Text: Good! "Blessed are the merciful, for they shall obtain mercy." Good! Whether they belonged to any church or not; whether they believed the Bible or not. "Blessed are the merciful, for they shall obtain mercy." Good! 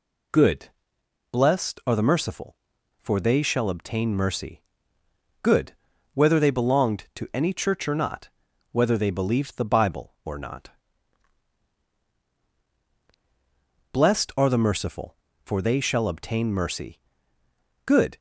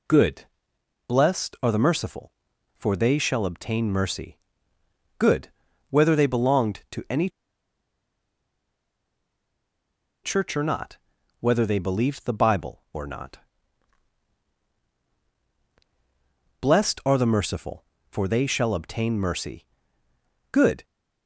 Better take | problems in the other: first | pauses between "any" and "church"; strong; at 7.2 s; 2.9 s long

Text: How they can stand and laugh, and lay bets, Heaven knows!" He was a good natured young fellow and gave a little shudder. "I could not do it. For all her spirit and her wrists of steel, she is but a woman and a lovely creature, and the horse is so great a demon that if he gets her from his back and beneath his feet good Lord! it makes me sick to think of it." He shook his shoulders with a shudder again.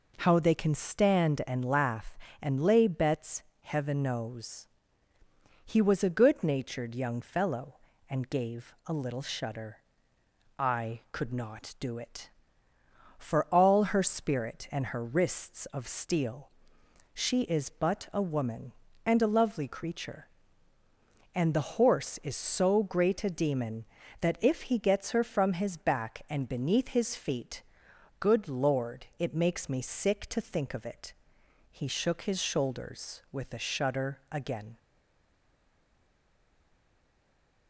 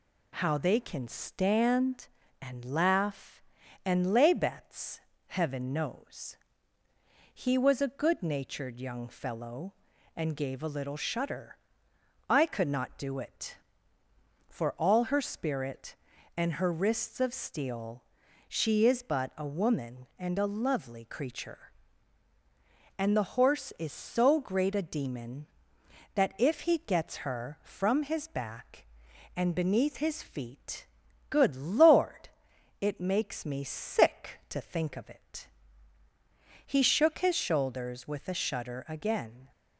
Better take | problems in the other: second | pauses between "feet" and "good"; noticeable; at 27.6 s; 0.58 s long; also in the second // stays silent after the last word; strong; from 34.7 s on; 2.9 s long

